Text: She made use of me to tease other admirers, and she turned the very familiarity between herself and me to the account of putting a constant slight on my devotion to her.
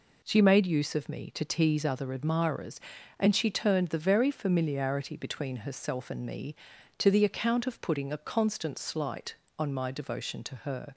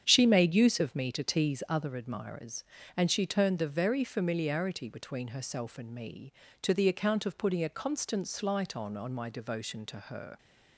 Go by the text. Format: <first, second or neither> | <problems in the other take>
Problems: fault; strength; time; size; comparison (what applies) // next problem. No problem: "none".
first | starts louder than the rest; strong; until 1.0 s; 8.5 dB // says "on" twice; at 8.9 s